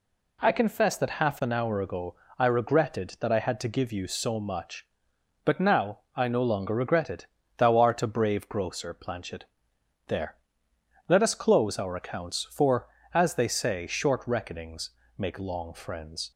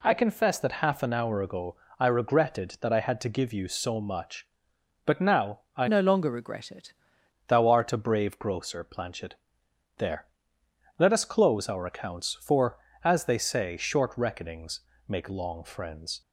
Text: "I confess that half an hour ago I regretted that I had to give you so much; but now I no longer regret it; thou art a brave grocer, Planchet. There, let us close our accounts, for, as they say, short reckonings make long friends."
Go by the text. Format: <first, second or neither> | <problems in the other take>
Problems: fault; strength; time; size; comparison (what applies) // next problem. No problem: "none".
first | pauses between "ago" and "I"; slight; at 1.7 s; 0.24 s long; slight in the first // pauses between "now" and "I"; slight; at 5.5 s; 0.16 s long; slight in the first // changes voice from "no" to "it"; from 5.8 to 6.9 s; 1.1 s long // pauses between "reckonings" and "make"; slight; at 14.7 s; 0.26 s long; slight in the first